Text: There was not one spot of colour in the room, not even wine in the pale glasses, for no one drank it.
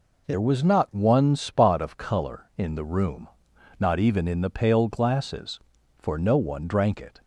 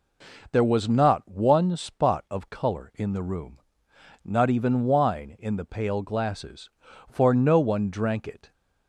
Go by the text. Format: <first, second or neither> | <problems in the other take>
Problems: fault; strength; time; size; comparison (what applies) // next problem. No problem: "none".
second | skips "wine"; at 4.2 s